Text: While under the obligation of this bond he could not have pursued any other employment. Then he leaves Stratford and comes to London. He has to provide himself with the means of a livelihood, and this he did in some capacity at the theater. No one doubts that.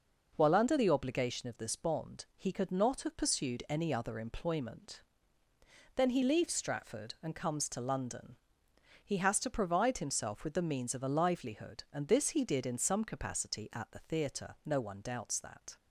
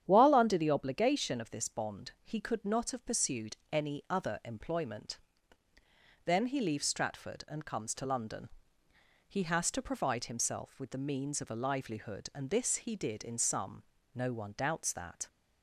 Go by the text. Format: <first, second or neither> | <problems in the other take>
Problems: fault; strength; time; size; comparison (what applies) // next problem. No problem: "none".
first | starts louder than the rest; strong; until 1.0 s; 9.5 dB // pauses between "pursued" and "any"; slight; at 3.5 s; 0.16 s long // skips "capacity at the theater"; at 13.9 s